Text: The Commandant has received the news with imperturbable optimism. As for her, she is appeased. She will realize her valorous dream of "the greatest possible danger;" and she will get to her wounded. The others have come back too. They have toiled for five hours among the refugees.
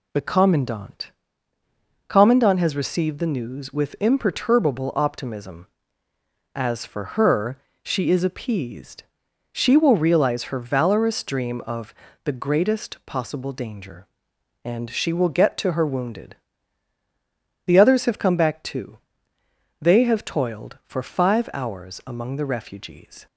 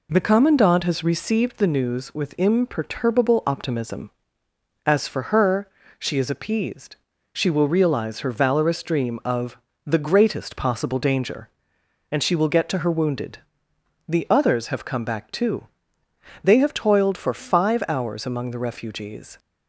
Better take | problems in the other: second | says "Commandant" twice; at 2.0 s // pauses between "of" and "the"; slight; at 11.9 s; 0.30 s long; slight in the second

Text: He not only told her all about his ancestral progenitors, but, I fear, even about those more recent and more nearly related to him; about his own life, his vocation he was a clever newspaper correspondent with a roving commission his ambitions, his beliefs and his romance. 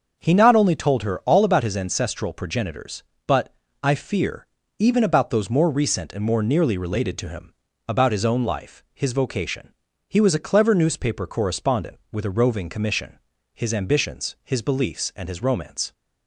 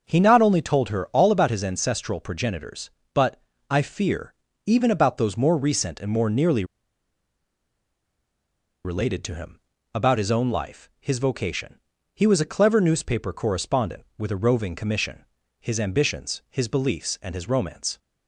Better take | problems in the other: first | starts louder than the rest; until 1.0 s; 6 dB; also in the first // pauses between "nearly" and "related"; strong; at 6.6 s; 2.2 s long // pauses between "vocation" and "he"; slight; at 11.7 s; 0.36 s long; slight in the first // pauses between "commission" and "his"; slight; at 15.2 s; 0.36 s long; slight in the first

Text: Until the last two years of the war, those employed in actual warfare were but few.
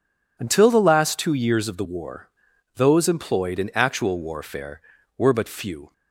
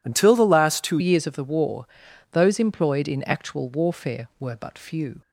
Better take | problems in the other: first | changes voice at "years"; from 0.9 s on; 4.3 s long

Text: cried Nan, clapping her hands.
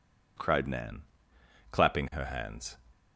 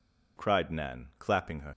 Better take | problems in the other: first | stops before "hands"; at 1.7 s

